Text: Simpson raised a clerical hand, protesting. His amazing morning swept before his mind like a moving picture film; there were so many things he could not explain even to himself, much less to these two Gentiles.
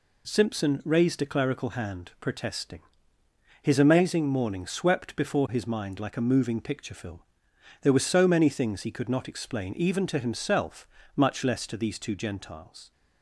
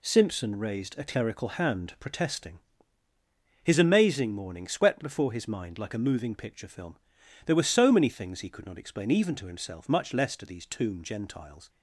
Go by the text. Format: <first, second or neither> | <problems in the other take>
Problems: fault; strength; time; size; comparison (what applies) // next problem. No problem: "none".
first | says "tomb" for "two"; at 10.6 s